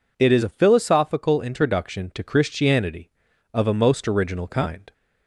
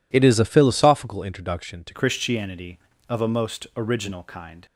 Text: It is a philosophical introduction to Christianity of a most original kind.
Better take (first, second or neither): first